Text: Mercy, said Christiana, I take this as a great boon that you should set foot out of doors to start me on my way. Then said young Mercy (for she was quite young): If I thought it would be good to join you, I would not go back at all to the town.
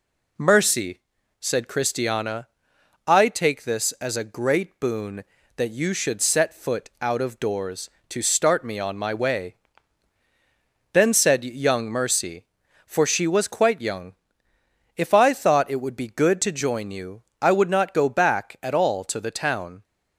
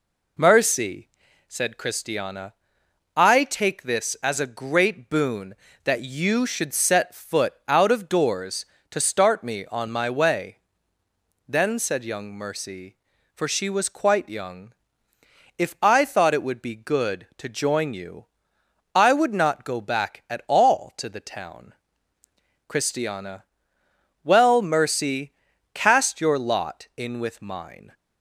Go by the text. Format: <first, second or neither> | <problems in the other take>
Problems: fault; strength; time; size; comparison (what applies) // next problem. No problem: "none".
first | goes on to say "Christiana Well Mercy cast your lot in with mine"; strong; from 22.6 s on; 5.2 s long